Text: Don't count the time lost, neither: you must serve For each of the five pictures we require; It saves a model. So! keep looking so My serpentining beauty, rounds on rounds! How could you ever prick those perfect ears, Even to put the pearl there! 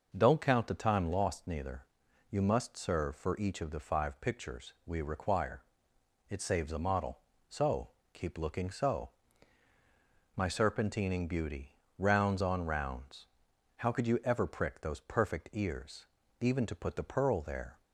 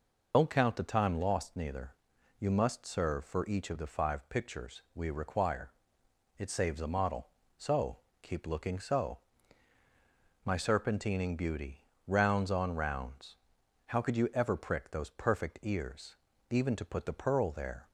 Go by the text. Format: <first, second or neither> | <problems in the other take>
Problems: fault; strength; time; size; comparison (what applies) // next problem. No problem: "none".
first | loses the start of "Don't"; at 0.3 s; 120 ms // pauses between "so" and "My"; strong; at 9.1 s; 1.2 s long; strong in the first